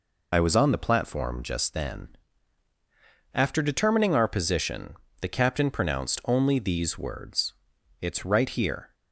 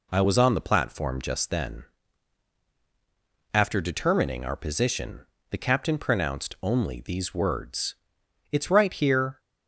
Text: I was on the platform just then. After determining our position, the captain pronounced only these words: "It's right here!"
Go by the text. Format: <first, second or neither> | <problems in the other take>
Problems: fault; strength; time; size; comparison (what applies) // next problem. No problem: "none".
second | loses the start of "I"; at 0.3 s; 60 ms